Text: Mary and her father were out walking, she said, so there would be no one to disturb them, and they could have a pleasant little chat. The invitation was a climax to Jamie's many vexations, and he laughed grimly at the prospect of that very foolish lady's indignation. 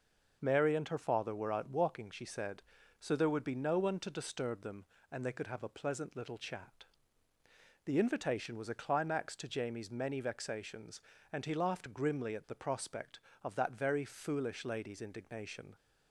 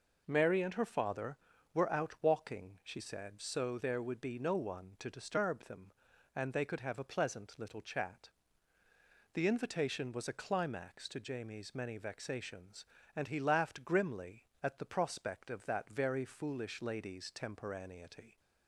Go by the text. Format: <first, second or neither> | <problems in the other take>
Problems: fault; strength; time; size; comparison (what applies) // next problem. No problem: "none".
first | says "temporaneity" for "indignation"; at 17.3 s